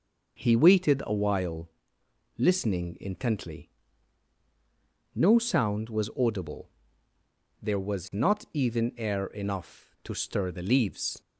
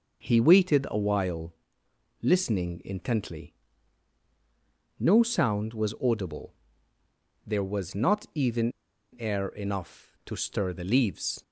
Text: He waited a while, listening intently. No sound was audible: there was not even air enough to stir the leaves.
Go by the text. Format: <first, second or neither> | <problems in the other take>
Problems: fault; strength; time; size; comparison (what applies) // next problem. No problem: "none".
first | pauses between "even" and "air"; noticeable; at 8.7 s; 0.46 s long